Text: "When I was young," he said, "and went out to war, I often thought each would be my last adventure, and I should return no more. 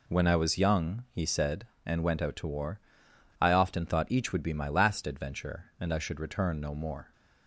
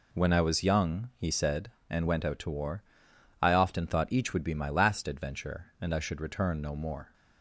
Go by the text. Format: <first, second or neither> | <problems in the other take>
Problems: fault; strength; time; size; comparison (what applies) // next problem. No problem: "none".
neither | none